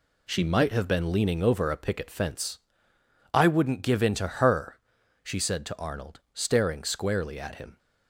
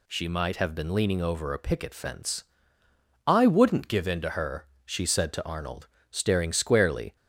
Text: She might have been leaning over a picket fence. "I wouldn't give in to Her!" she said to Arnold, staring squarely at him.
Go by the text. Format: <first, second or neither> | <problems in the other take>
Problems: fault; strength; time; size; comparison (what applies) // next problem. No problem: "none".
first | stops before "at him"; at 7.1 s